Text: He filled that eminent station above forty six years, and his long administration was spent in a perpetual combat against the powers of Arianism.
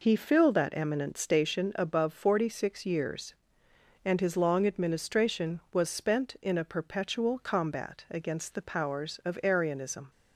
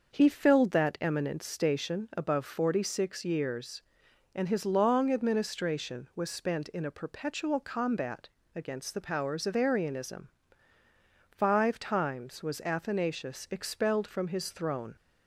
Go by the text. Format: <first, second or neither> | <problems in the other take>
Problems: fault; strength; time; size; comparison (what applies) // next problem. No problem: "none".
first | starts louder than the rest; until 1.1 s; 6 dB // pauses between "combat" and "against"; slight; at 8.2 s; 0.26 s long // goes on to say "Five times was Athanasius expelled from his throne"; strong; from 11.2 s on; 3.6 s long